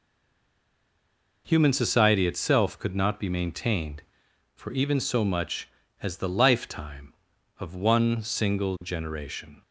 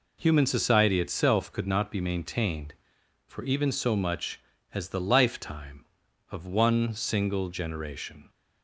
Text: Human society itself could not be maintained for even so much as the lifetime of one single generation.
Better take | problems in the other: second | stays silent before the first word; noticeable; until 1.4 s; 1.4 s long

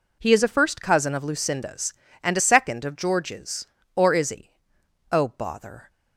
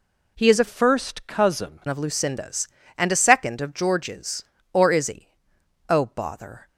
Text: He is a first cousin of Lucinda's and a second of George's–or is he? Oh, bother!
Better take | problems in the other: first | changes voice from "first" to "cousin"; from 0.6 to 1.8 s; 1.2 s long

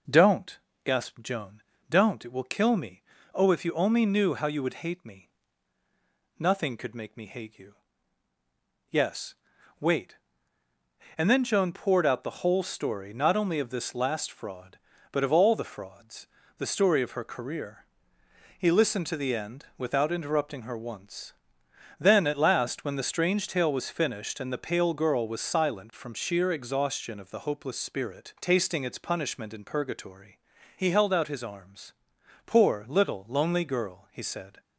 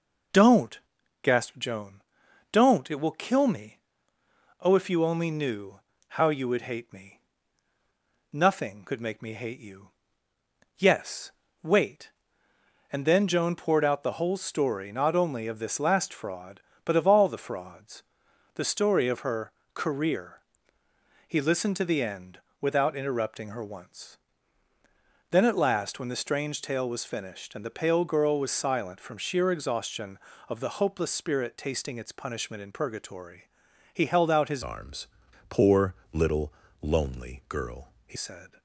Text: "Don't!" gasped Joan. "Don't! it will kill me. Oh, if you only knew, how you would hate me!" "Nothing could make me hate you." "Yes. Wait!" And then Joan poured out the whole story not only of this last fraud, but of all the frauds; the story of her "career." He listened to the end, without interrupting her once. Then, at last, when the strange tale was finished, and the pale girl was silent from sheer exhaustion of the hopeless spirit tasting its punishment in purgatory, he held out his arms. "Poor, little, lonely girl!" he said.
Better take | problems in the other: first | pauses between "her" and "career"; slight; at 19.5 s; 0.24 s long // changes voice from "arms" to "he"; from 34.6 to 38.1 s; 3.5 s long

